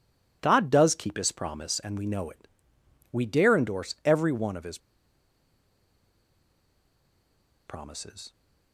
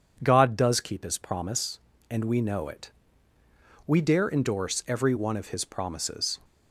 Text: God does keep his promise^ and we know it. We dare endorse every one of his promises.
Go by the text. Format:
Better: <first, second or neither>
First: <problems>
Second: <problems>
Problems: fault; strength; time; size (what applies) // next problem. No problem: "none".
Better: second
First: pauses between "his" and "promises"; strong; at 4.7 s; 2.8 s long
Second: none